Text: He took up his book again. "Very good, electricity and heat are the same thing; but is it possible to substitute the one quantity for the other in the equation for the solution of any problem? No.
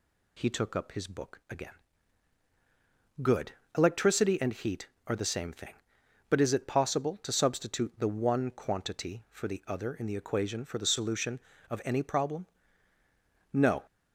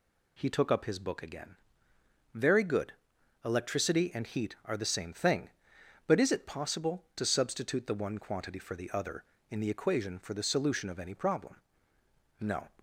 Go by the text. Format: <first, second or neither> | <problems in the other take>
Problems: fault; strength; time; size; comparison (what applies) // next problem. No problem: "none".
second | skips "Very"; at 2.4 s